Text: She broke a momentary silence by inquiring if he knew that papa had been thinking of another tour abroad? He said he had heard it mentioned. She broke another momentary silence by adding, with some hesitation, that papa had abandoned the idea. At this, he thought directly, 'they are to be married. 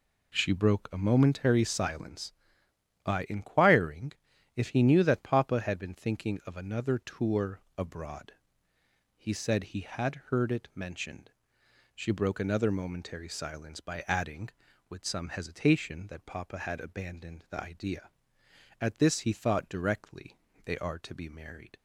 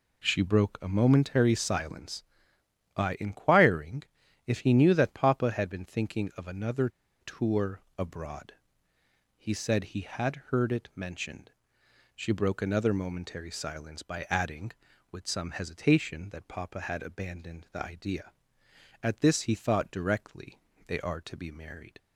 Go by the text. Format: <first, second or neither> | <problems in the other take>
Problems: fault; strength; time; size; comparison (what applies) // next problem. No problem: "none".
first | pauses between "inquiring" and "if"; at 4.0 s; 0.42 s long; also in the first // pauses between "another" and "tour"; slight; at 6.8 s; 0.32 s long // pauses between "tour" and "abroad"; slight; at 7.8 s; 0.16 s long; slight in the first